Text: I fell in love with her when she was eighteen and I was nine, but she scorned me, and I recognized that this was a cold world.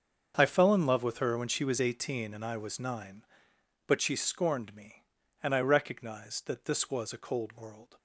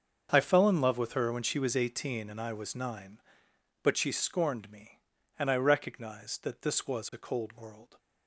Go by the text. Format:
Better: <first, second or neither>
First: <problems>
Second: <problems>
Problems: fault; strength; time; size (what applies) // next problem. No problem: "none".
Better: neither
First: starts louder than the rest; until 1.3 s; 7 dB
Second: starts louder than the rest; until 1.3 s; 7 dB